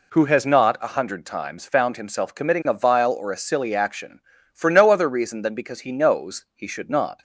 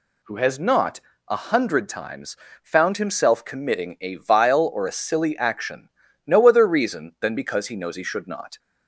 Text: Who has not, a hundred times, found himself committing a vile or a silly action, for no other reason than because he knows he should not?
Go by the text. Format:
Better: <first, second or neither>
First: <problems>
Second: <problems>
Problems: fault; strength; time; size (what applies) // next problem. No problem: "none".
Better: first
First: none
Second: skips "for"; at 6.0 s